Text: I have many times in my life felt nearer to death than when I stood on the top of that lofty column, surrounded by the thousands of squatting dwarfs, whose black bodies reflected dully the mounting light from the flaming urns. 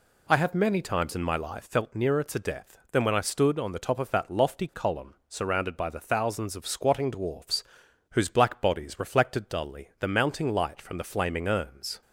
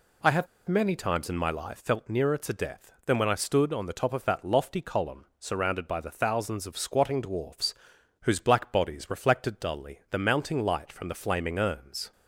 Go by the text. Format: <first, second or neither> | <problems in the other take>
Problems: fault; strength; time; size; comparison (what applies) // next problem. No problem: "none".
first | pauses between "have" and "many"; slight; at 0.4 s; 0.21 s long